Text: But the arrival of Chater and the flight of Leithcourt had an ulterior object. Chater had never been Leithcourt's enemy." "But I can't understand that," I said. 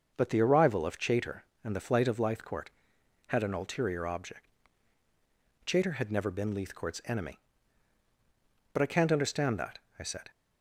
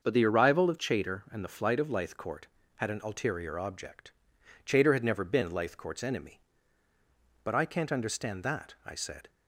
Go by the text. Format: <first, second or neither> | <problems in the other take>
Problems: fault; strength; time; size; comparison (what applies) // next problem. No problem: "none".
neither | starts louder than the rest; the same in both